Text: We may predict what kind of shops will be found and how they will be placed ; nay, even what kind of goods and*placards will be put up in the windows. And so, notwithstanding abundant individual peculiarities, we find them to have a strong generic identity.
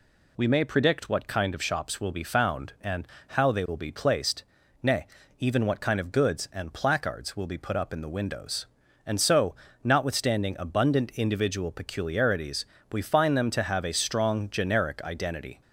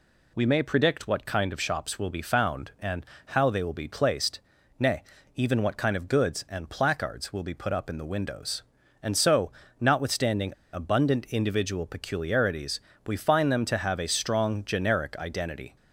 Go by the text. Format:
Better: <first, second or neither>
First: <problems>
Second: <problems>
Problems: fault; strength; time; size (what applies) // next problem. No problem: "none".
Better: first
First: pauses between "and" and "how"; slight; at 3.0 s; 0.22 s long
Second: pauses between "and" and "how"; slight; at 3.0 s; 0.22 s long // pauses between "notwithstanding" and "abundant"; slight; at 10.5 s; 0.22 s long